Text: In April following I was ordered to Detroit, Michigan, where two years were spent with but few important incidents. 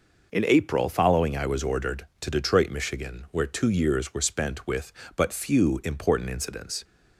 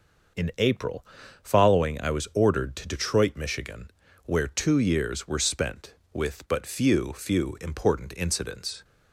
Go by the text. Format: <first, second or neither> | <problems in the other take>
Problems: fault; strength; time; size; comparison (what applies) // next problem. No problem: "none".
first | starts louder than the rest; until 1.8 s; 6 dB // pauses between "April" and "following"; at 1.0 s; 0.38 s long // says "few" twice; at 7.1 s